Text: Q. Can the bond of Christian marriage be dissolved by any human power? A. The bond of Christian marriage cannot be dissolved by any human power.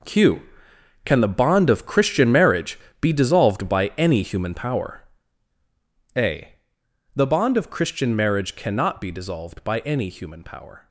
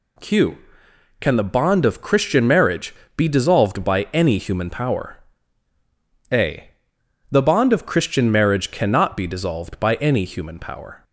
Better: second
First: gets quieter; strong; throughout; 13 dB // pauses between "marriage" and "be"; slight; at 2.7 s; 0.22 s long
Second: pauses between "marriage" and "be"; slight; at 2.9 s; 0.22 s long

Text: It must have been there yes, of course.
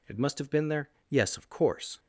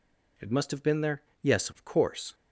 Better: neither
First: pauses between "there" and "yes"; slight; at 0.8 s; 0.18 s long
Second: pauses between "there" and "yes"; slight; at 1.2 s; 0.18 s long

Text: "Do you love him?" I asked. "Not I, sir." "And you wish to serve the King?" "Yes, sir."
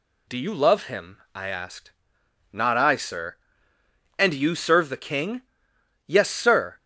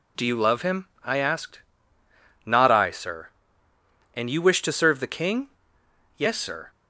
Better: second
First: skips "wish to"; at 4.5 s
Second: none

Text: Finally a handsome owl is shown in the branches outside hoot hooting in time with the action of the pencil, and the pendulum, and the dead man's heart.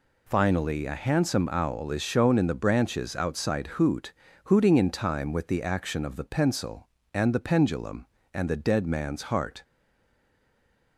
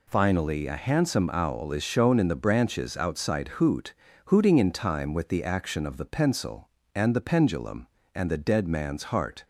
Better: second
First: pauses between "hoot" and "hooting"; slight; at 4.1 s; 0.34 s long // stays silent after the last word; noticeable; from 9.6 s on; 1.3 s long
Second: pauses between "hoot" and "hooting"; slight; at 3.9 s; 0.34 s long

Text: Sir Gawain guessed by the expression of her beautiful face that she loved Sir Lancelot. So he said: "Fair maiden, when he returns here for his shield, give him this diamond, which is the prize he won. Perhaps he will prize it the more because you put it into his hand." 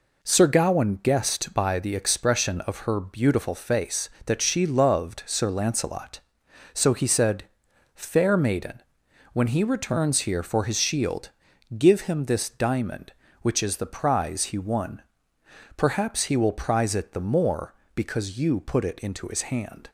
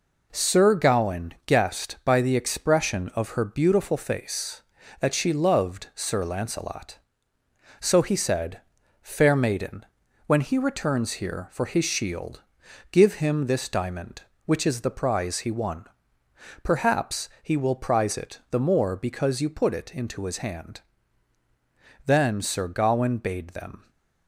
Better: first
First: none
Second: goes on to say "Then Sir Gawain bade them"; strong; from 22.0 s on; 1.8 s long

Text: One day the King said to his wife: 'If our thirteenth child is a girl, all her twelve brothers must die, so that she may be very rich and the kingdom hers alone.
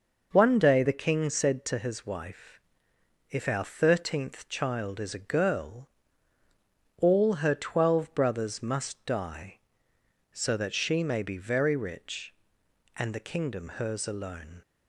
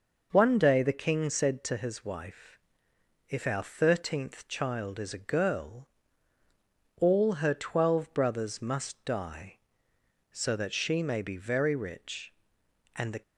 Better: first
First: none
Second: stops before "kingdom hers alone"; at 13.2 s

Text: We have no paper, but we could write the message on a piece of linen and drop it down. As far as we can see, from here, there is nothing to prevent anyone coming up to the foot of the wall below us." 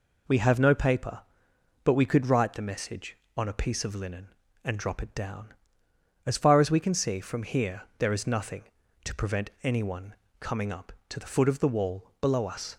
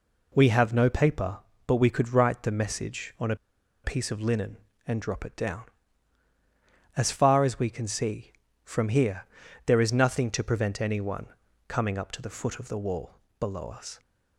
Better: first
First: pauses between "anyone" and "coming"; slight; at 10.1 s; 0.26 s long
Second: pauses between "a" and "piece"; noticeable; at 3.3 s; 0.49 s long // pauses between "anyone" and "coming"; at 11.2 s; 0.42 s long // pauses between "wall" and "below"; slight; at 13.1 s; 0.28 s long

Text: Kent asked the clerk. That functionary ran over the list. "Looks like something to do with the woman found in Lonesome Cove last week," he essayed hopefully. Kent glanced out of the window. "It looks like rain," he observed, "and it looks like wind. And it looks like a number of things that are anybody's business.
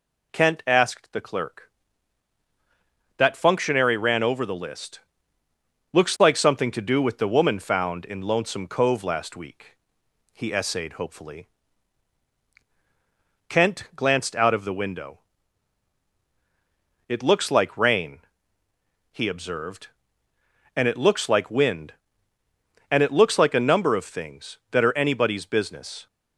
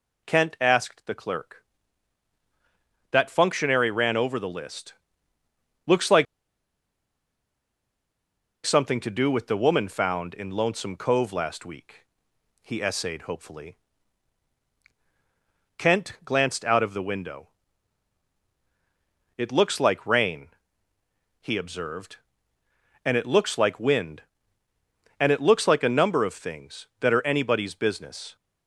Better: first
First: none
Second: pauses between "like" and "something"; strong; at 6.2 s; 2.4 s long

